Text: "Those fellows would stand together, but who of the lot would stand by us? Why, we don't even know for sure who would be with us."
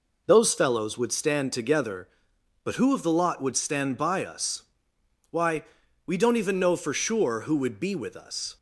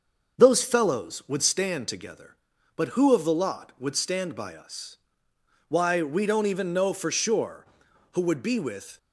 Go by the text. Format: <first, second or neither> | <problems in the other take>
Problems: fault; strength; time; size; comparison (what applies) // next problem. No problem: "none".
first | starts louder than the rest; until 1.4 s; 6 dB // stops before "us"; at 8.9 s